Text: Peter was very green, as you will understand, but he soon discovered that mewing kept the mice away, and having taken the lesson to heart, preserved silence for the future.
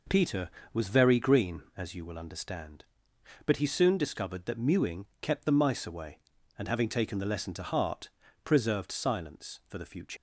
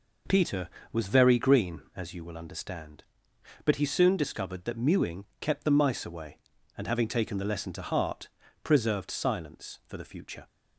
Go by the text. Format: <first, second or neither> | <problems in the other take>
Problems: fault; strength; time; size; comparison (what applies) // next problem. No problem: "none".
second | leaves "future" unfinished; at 10.1 s; 105 ms